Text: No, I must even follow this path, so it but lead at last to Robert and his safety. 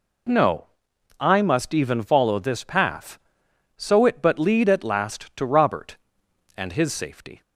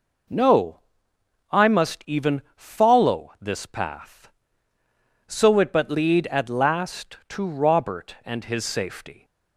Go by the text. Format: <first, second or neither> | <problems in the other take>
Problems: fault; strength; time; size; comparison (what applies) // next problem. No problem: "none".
neither | none